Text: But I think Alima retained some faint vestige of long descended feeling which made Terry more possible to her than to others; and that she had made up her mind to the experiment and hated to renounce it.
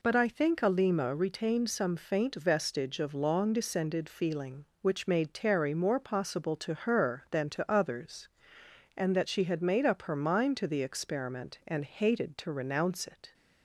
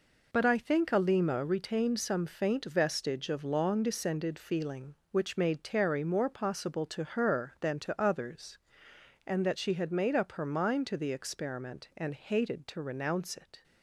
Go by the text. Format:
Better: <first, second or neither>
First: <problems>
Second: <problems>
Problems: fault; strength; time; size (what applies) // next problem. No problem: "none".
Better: first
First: none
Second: gets quieter; strong; throughout; 8.5 dB